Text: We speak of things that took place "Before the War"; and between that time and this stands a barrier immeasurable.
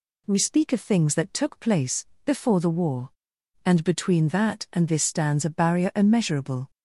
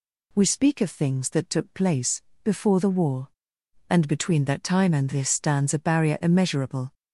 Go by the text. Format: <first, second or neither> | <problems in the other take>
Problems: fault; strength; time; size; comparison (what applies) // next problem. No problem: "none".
second | pauses between "place" and "Before"; slight; at 2.0 s; 0.20 s long; slight in the second // skips "time"; at 4.6 s